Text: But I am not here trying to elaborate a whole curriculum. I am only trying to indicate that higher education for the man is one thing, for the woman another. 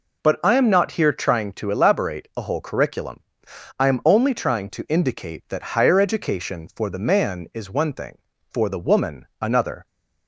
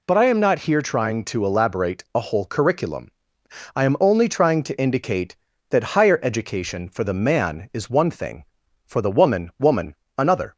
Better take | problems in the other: first | says "woman" twice; at 9.5 s

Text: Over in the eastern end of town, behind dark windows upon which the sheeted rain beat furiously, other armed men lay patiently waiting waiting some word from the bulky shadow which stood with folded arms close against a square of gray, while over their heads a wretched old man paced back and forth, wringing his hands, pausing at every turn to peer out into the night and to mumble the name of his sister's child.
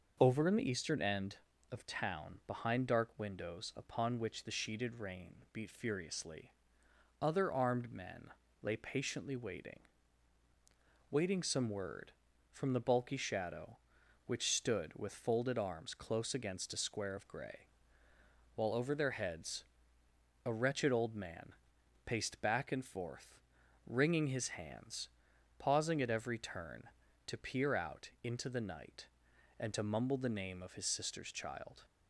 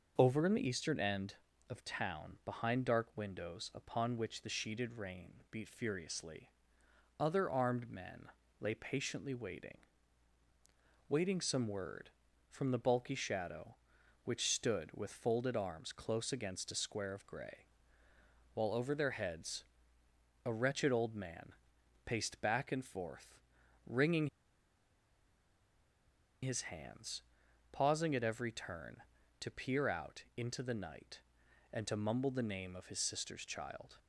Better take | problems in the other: first | starts louder than the rest; noticeable; until 1.1 s; 6 dB; noticeable in the first // pauses between "men" and "lay"; slight; at 8.2 s; 0.32 s long; slight in the first // pauses between "waiting" and "waiting"; strong; at 9.7 s; 1.3 s long; strong in the first // pauses between "heads" and "a"; noticeable; at 19.6 s; 0.82 s long; noticeable in the first // pauses between "man" and "paced"; noticeable; at 21.5 s; 0.52 s long; noticeable in the first // pauses between "wringing" and "his"; strong; at 24.2 s; 2.1 s long // pauses between "out" and "into"; slight; at 30.2 s; 0.16 s long; slight in the first

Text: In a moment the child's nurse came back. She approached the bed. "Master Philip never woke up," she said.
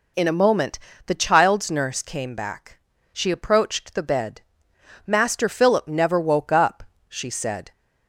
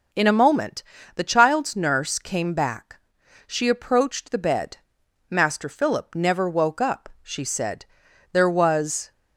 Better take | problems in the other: first | pauses between "moment" and "the"; slight; at 0.8 s; 0.32 s long; slight in the first // goes on to say "There was"; noticeable; from 8.3 s on; 0.78 s long

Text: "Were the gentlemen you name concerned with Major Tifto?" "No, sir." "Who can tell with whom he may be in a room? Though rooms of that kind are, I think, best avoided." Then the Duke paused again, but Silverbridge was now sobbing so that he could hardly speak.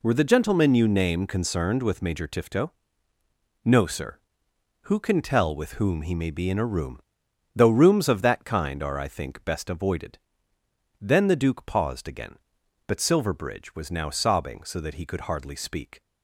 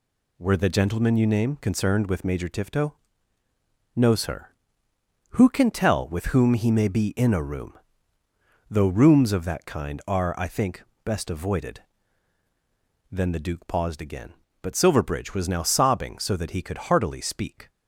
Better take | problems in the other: first | says "heartily" for "hardly"; at 16.7 s

